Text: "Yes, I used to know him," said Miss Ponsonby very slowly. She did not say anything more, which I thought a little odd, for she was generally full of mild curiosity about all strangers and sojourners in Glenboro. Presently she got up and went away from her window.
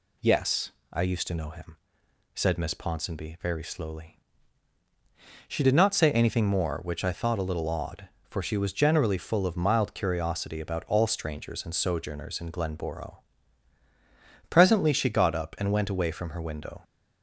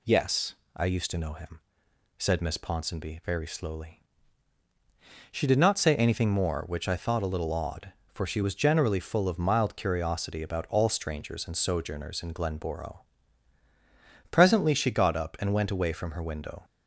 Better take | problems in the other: neither | none

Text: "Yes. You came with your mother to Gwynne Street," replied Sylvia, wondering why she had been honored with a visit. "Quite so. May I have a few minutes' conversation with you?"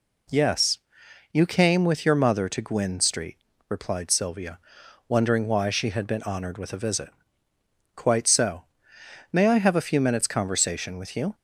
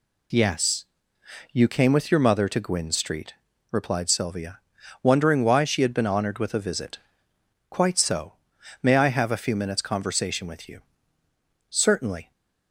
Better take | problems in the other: first | goes on to say "Certainly"; noticeable; from 11.6 s on; 0.62 s long

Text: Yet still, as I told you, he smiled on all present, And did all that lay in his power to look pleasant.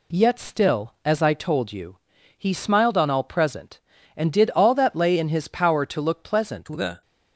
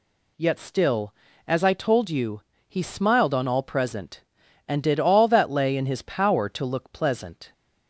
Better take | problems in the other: second | goes on to say "The"; slight; from 6.6 s on; 0.36 s long

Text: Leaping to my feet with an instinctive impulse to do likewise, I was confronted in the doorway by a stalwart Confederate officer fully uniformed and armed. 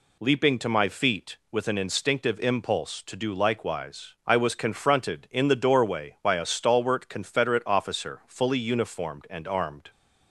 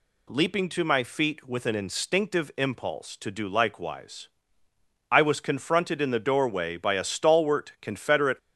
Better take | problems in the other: first | stops before "officer fully uniformed and armed"; at 8.3 s

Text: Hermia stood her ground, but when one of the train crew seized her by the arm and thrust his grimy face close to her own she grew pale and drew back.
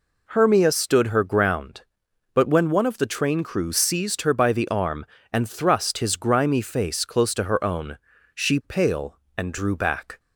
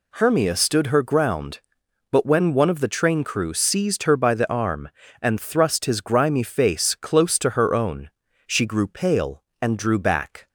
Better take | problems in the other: second | pauses between "own" and "she"; at 7.9 s; 0.38 s long; slight in the second // skips "grew"; at 8.6 s

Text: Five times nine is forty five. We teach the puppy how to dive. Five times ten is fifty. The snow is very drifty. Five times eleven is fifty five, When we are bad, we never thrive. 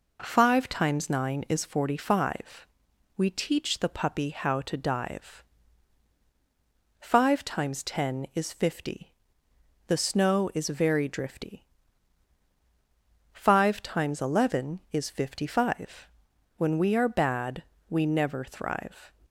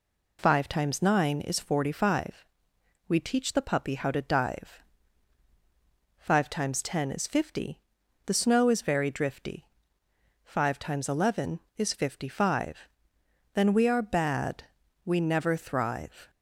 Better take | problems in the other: first | says "Then" for "When"; at 13.5 s

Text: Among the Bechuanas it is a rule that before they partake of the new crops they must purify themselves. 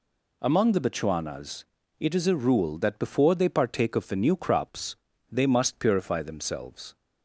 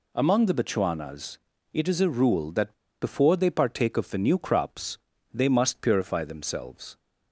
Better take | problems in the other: first | pauses between "Bechuanas" and "it"; slight; at 1.3 s; 0.34 s long; slight in the first // pauses between "that" and "before"; slight; at 2.7 s; 0.29 s long // pauses between "crops" and "they"; slight; at 4.9 s; 0.34 s long; slight in the first

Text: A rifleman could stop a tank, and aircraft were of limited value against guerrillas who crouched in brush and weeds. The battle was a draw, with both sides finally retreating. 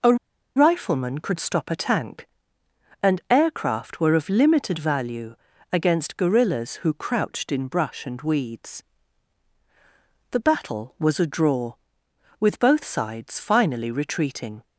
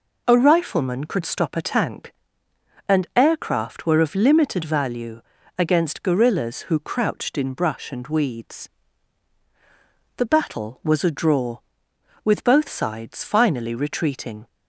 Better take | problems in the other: second | pauses between "A" and "rifleman"; at 0.1 s; 0.41 s long // pauses between "value" and "against"; at 5.3 s; 0.38 s long; also in the second

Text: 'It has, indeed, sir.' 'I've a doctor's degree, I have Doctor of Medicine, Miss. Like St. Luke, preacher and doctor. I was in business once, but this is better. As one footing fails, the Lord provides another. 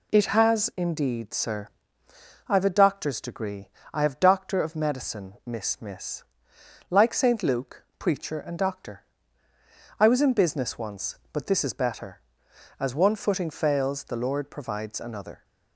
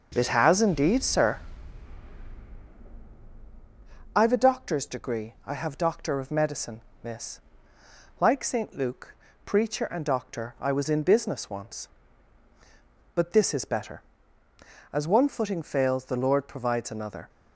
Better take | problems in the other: second | says "Miss" twice; at 5.7 s

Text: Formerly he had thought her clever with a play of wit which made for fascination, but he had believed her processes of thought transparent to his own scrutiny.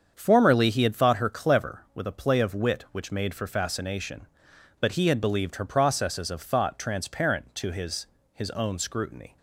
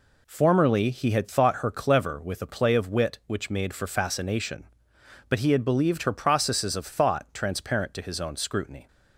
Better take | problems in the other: second | starts louder than the rest; strong; until 1.1 s; 7.5 dB // says "his" twice; at 8.3 s

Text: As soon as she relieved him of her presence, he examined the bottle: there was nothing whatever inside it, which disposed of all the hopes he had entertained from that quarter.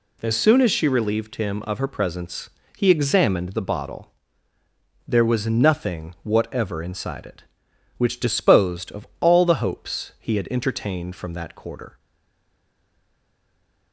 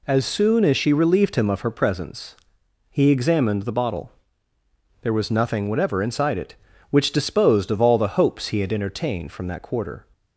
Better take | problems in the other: second | stays silent after the last word; noticeable; from 11.9 s on; 2.0 s long

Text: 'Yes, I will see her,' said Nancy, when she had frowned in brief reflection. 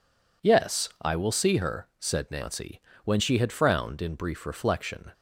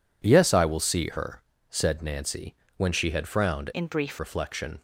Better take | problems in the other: first | changes voice from "in" to "brief"; from 3.7 to 4.1 s; 0.4 s long

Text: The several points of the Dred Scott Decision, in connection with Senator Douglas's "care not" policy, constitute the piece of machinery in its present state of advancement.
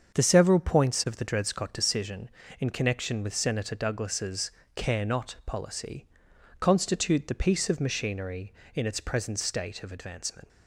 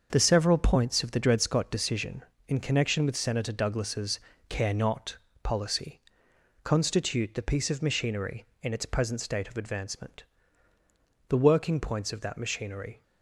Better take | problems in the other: first | starts louder than the rest; until 1.1 s; 6.5 dB; also in the first // pauses between "Douglas's" and "care"; slight; at 4.1 s; 0.30 s long; slight in the first // pauses between "not" and "policy"; slight; at 5.1 s; 0.26 s long // goes on to say "The working points of that machinery"; strong; from 11.2 s on; 1.7 s long

